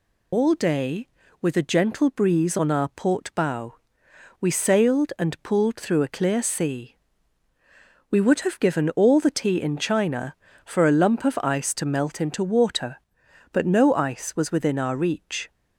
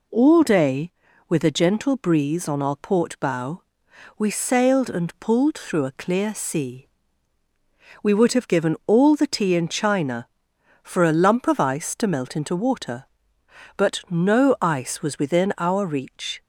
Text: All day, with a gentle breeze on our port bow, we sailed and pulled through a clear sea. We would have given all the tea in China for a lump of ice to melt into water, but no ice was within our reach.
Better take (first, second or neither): second